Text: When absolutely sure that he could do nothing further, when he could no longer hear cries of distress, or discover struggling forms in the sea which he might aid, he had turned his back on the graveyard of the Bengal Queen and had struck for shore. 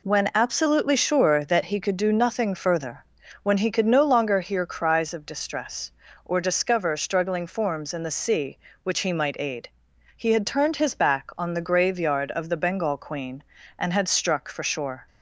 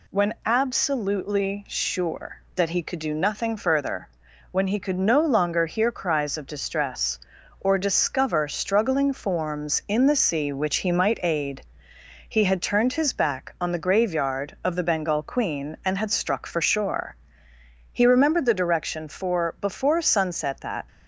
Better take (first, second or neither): first